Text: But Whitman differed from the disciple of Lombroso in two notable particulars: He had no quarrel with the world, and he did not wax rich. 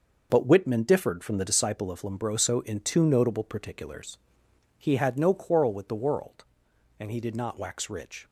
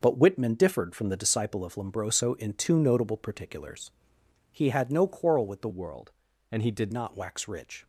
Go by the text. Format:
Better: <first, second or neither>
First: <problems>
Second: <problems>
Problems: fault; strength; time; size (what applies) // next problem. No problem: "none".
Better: first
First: none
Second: starts louder than the rest; noticeable; until 1.0 s; 6 dB // changes voice from "world" to "did"; from 5.6 to 6.9 s; 1.3 s long